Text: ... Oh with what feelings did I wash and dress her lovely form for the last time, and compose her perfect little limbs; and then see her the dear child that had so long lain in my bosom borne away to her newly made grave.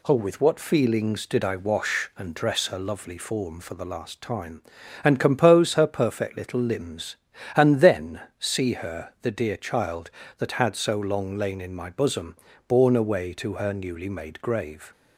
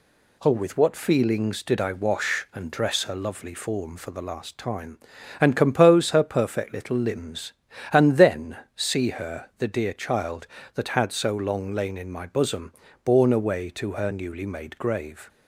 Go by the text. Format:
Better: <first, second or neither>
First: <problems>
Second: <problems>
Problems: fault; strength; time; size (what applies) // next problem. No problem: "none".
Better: neither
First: pauses between "then" and "see"; slight; at 8.1 s; 0.18 s long // pauses between "bosom" and "borne"; slight; at 12.3 s; 0.32 s long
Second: pauses between "then" and "see"; slight; at 8.5 s; 0.18 s long // pauses between "bosom" and "borne"; slight; at 12.7 s; 0.32 s long